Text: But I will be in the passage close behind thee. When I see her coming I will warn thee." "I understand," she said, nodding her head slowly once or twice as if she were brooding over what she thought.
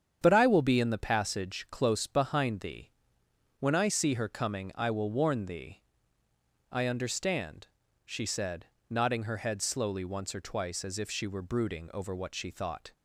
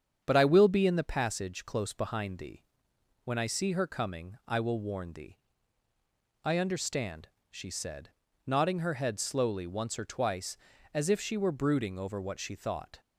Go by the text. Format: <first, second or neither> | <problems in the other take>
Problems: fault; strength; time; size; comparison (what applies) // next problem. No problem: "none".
neither | starts louder than the rest; strong; the same in both